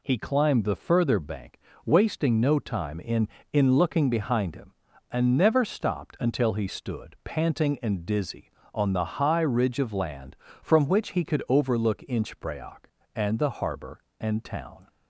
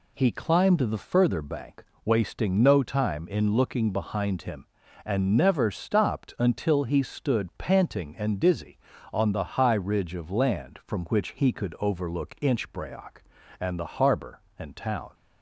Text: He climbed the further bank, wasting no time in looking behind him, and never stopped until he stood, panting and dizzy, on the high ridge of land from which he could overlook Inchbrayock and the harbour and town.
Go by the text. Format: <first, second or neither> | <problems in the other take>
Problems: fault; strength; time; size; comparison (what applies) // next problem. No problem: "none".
second | says "in" twice; at 3.5 s